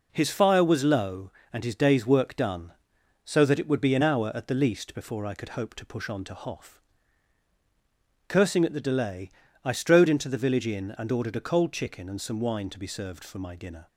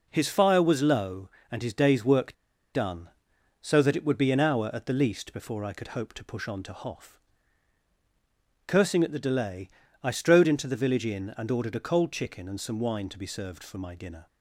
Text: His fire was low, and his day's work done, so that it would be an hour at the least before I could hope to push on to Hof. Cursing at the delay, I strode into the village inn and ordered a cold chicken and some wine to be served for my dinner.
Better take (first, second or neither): first